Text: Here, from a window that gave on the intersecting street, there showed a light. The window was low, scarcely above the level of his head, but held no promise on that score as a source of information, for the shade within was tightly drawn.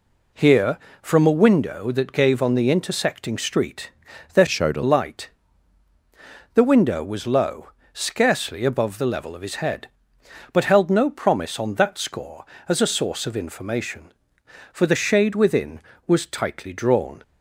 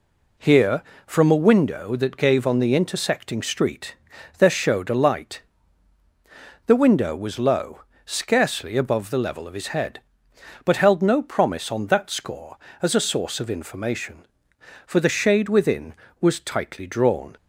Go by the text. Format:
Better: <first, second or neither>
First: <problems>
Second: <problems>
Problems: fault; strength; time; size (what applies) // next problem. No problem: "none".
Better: second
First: changes voice from "showed" to "a"; from 4.4 to 4.8 s; 0.4 s long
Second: none